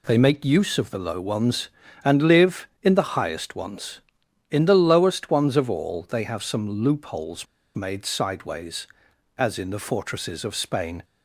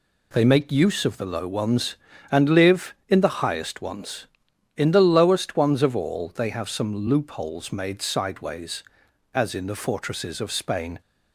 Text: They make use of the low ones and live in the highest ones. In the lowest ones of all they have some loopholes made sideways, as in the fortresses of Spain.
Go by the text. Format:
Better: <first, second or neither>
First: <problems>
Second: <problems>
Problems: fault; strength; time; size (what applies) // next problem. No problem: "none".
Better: second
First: pauses between "loopholes" and "made"; slight; at 7.4 s; 0.30 s long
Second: none